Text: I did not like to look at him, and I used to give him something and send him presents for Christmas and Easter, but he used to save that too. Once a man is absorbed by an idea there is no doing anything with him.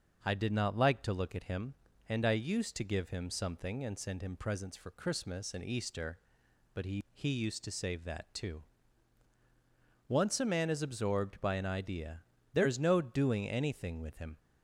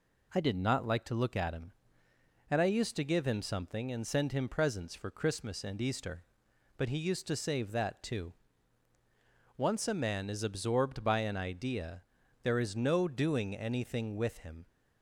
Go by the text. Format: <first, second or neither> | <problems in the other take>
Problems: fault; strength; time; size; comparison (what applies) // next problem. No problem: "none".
second | starts louder than the rest; until 1.2 s; 6 dB // says "he" twice; at 7.1 s // pauses between "idea" and "there"; slight; at 12.2 s; 0.32 s long; also in the second